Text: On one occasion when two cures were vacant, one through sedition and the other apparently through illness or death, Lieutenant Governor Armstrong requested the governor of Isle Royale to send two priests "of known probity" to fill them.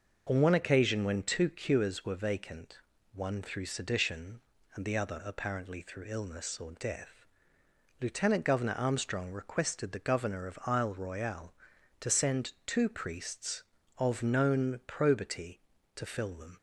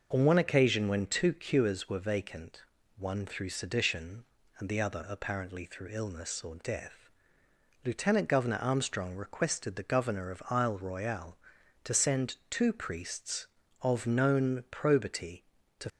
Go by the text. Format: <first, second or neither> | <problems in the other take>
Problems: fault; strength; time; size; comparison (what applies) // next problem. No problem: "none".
first | stops before "fill them"; at 15.8 s